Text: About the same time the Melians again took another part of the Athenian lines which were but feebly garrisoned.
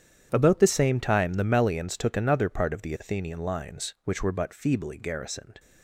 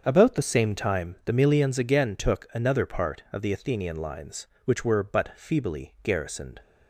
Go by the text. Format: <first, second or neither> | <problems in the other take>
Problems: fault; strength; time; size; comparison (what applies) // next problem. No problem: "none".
second | starts louder than the rest; strong; until 1.3 s; 9 dB; also in the second // skips "again"; at 1.9 s